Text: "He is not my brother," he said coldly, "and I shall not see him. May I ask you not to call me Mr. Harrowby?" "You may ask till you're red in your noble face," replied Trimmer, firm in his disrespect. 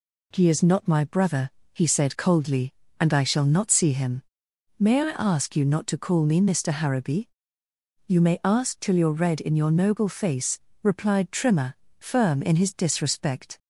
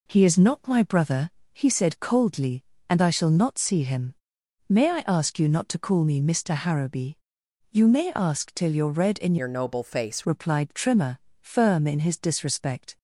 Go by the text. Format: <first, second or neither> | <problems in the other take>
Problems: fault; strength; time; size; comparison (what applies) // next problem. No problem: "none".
first | changes voice from "your" to "face"; from 9.3 to 10.2 s; 0.9 s long